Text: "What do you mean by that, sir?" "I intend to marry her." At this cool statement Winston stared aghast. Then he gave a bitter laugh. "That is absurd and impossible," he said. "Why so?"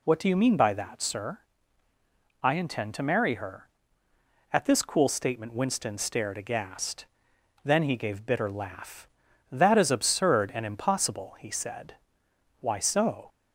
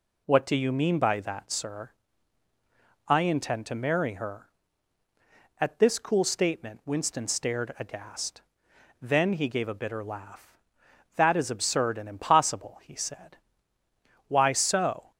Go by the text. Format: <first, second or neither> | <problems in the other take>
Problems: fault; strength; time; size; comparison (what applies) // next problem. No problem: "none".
second | skips "a"; at 8.2 s